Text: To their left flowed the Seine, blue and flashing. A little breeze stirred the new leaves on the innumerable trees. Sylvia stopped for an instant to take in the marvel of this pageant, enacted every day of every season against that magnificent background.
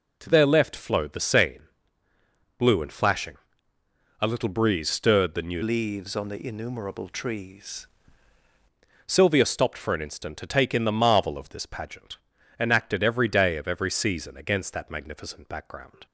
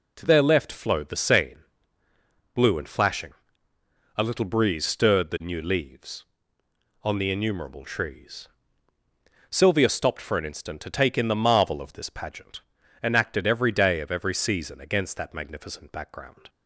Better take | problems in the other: second | changes voice from "leaves" to "trees"; from 5.6 to 7.8 s; 2.2 s long

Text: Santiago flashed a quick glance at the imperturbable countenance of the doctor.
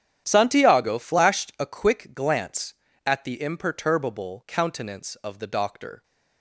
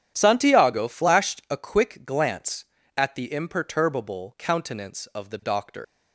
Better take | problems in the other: first | starts louder than the rest; strong; until 1.1 s; 9.5 dB; strong in the first // leaves "doctor" unfinished; at 5.8 s; 110 ms

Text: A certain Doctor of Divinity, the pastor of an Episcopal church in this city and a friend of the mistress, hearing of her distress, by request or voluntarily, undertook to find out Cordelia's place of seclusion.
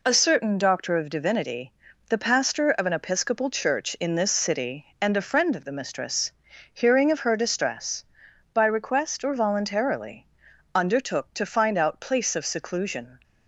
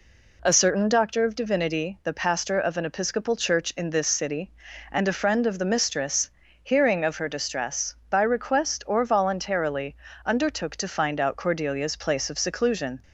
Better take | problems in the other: second | skips "Cordelia's"; at 11.9 s

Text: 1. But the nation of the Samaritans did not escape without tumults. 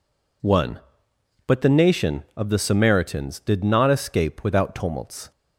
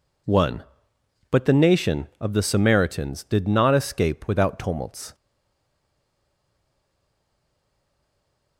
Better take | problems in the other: first | stays silent after the last word; strong; from 5.1 s on; 3.4 s long

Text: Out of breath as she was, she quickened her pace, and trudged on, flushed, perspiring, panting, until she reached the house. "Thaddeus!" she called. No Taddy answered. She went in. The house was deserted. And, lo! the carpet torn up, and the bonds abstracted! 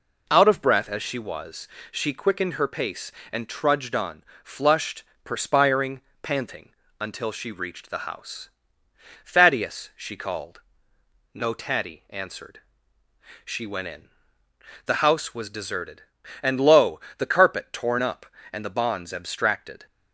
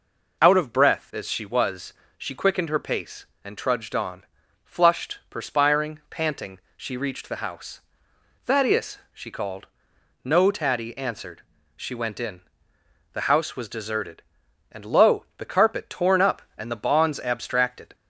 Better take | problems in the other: first | skips "until"; at 6.6 s

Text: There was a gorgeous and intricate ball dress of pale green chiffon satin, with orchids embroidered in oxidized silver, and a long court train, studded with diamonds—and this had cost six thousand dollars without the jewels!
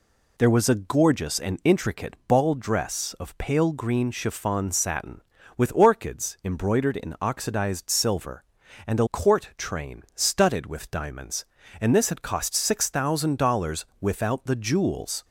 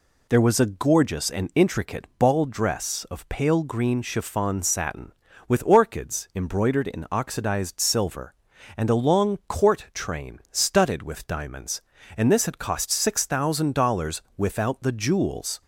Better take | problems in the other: second | skips "long"; at 9.0 s // pauses between "dollars" and "without"; slight; at 13.8 s; 0.16 s long; slight in the second

